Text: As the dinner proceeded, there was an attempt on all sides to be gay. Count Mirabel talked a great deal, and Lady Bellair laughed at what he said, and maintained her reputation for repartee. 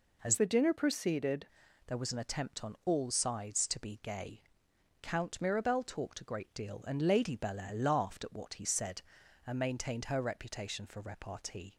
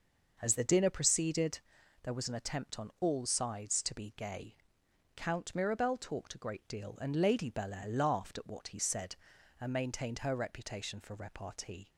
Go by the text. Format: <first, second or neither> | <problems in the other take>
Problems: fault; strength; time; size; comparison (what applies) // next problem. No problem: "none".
second | changes voice from "the" to "proceeded"; from 0.3 to 1.4 s; 1.1 s long